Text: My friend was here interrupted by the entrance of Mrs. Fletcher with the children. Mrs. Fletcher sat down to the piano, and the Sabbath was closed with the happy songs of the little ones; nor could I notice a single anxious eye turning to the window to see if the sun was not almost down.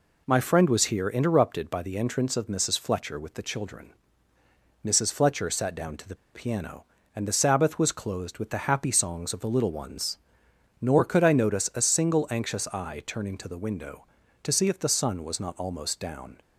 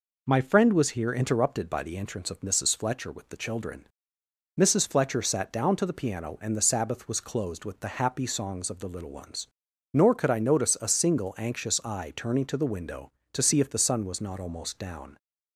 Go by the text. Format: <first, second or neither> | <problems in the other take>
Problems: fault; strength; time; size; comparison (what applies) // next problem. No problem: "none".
second | pauses between "the" and "piano"; slight; at 6.1 s; 0.18 s long